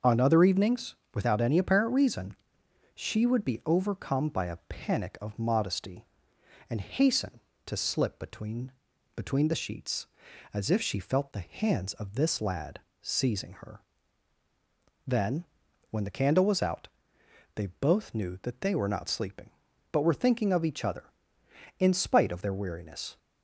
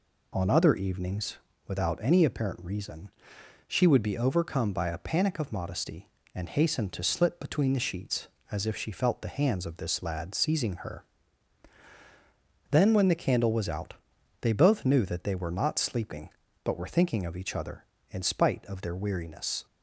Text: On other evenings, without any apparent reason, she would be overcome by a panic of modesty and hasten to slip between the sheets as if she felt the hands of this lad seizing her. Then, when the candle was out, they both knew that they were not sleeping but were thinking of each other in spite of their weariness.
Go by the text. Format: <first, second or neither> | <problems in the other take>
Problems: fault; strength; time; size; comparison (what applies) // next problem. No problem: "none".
second | starts louder than the rest; noticeable; until 1.2 s; 6 dB // says "between" twice; at 9.1 s // pauses between "lad" and "seizing"; slight; at 12.7 s; 0.22 s long